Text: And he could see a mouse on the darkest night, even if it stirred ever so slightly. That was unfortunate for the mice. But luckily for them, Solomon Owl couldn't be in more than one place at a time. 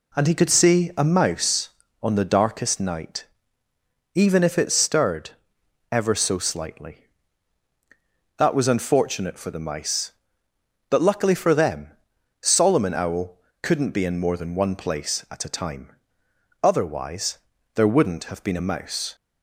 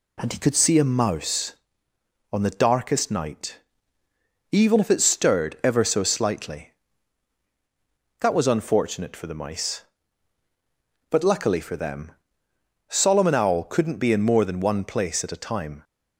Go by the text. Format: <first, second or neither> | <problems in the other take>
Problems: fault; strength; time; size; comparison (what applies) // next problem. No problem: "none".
second | pauses between "stirred" and "ever"; noticeable; at 5.2 s; 0.60 s long // pauses between "Owl" and "couldn't"; slight; at 13.3 s; 0.24 s long // goes on to say "Otherwise there wouldn't have been a mouse"; strong; from 16.6 s on; 2.5 s long